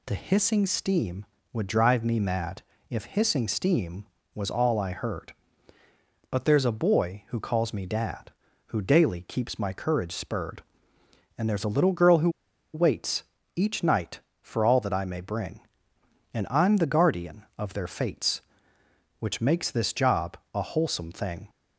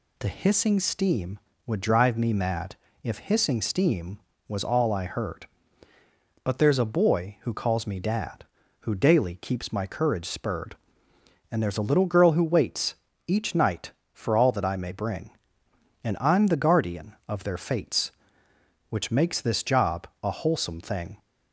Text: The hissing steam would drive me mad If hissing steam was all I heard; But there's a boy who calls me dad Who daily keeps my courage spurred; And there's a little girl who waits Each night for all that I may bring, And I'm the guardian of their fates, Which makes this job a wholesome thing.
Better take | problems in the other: second | pauses between "mad" and "If"; slight; at 2.6 s; 0.28 s long; slight in the second // pauses between "who" and "waits"; at 12.2 s; 0.44 s long // pauses between "waits" and "Each"; slight; at 13.2 s; 0.32 s long; slight in the second // pauses between "job" and "a"; slight; at 20.3 s; 0.16 s long

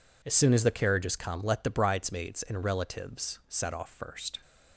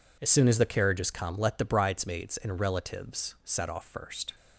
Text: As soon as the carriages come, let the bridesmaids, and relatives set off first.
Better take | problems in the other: neither | none

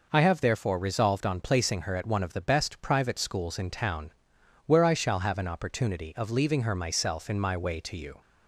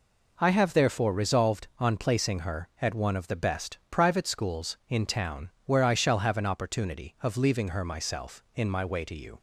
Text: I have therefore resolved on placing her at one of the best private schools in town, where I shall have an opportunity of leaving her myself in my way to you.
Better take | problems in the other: neither | none

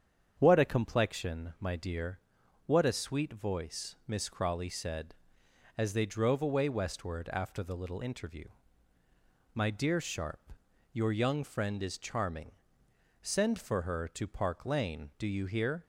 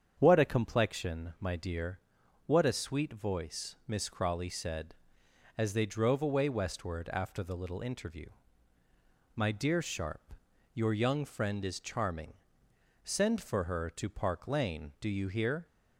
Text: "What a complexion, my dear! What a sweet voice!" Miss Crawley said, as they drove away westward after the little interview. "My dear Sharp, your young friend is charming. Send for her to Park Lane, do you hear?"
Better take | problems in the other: neither | starts louder than the rest; strong; the same in both

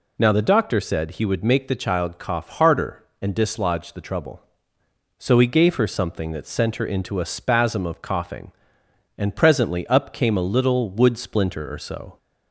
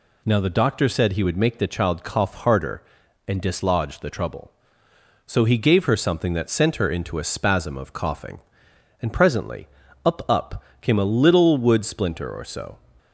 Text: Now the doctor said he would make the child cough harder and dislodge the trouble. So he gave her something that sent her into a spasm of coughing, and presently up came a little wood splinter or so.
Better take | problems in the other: first | pauses between "presently" and "up"; at 9.6 s; 0.38 s long // says "up" twice; at 10.2 s

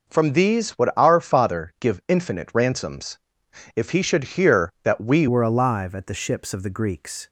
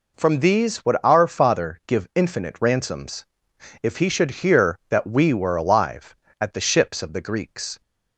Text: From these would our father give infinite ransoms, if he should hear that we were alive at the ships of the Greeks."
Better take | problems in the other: second | changes voice at "were"; from 5.2 s on; 2.0 s long

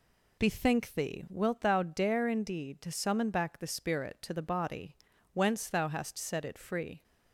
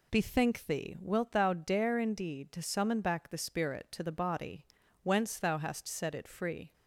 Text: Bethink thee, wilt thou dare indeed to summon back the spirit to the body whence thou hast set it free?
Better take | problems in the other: neither | pauses between "body" and "whence"; the same in both

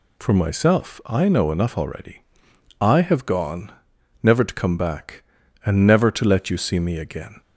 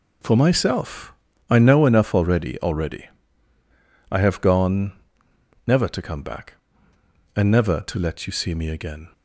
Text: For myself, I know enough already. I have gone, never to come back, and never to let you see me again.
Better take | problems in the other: first | says "already" twice; at 2.6 s

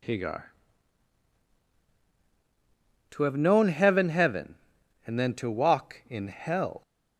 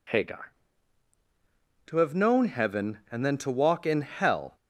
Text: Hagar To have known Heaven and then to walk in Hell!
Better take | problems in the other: second | says "Heaven" twice; at 4.0 s

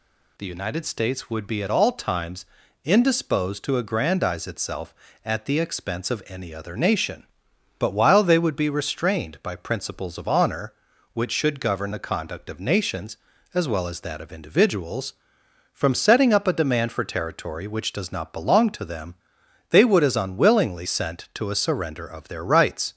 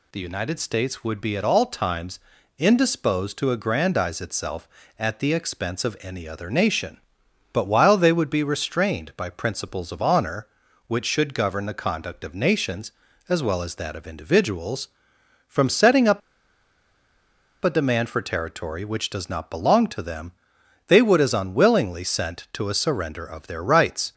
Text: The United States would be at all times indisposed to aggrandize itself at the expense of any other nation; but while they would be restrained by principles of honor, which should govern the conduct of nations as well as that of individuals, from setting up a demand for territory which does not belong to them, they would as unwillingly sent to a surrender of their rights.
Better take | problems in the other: first | pauses between "times" and "indisposed"; at 2.1 s; 0.38 s long; also in the first // pauses between "up" and "a"; strong; at 16.2 s; 1.4 s long

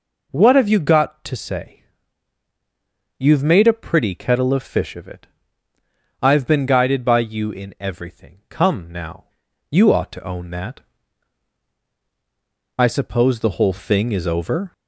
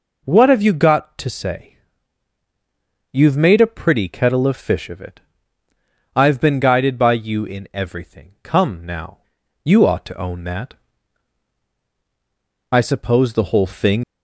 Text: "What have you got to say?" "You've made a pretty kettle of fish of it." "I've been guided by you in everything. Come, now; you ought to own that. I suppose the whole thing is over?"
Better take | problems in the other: first | stops before "is over"; at 14.0 s

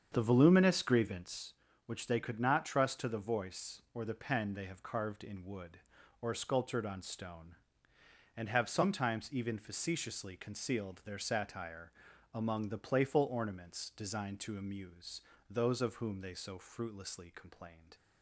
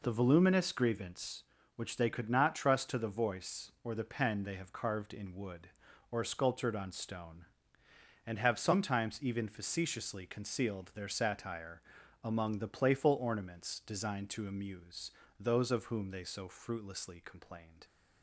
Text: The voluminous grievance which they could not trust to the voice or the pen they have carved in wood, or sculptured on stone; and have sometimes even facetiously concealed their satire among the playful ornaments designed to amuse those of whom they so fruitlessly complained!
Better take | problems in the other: second | starts louder than the rest; strong; until 1.4 s; 7.5 dB // pauses between "satire" and "among"; at 11.9 s; 0.40 s long; also in the second // pauses between "amuse" and "those"; slight; at 15.2 s; 0.28 s long; slight in the second

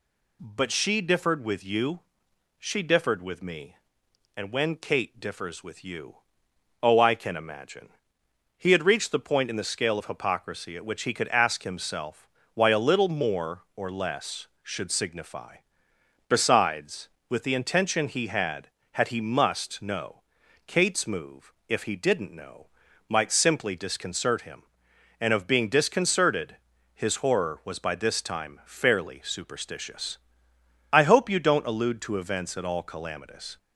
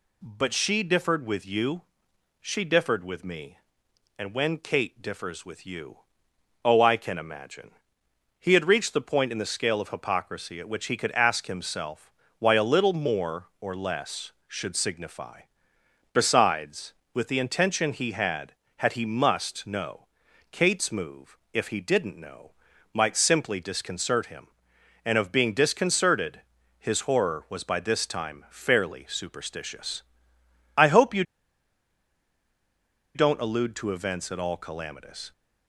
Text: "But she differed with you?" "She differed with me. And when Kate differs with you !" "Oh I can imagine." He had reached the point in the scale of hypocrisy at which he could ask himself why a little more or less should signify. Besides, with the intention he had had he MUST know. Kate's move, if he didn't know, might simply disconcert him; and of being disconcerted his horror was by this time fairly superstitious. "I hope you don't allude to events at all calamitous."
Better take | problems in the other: first | pauses between "himself" and "why"; slight; at 12.1 s; 0.26 s long; slight in the first // pauses between "disconcerted" and "his"; slight; at 26.4 s; 0.36 s long; slight in the first // pauses between "you" and "don't"; strong; at 31.2 s; 1.9 s long

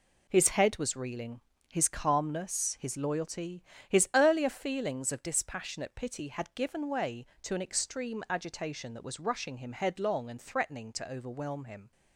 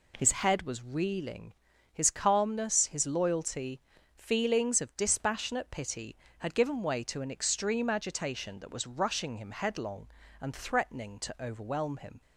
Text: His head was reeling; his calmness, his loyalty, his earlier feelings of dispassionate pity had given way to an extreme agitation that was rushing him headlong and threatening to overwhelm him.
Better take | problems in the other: first | skips "his earlier"; at 3.9 s

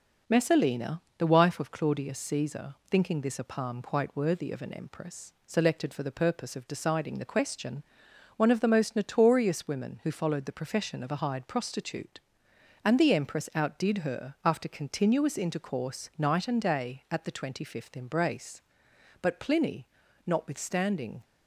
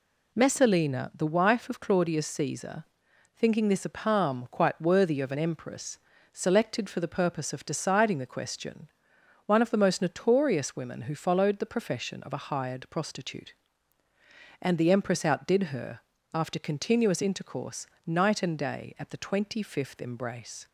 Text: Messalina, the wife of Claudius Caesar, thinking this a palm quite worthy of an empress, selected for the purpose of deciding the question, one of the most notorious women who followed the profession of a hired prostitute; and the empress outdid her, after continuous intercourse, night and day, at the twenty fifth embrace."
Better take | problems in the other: second | goes on to say "But Pliny notwithstanding"; strong; from 19.1 s on; 2.0 s long

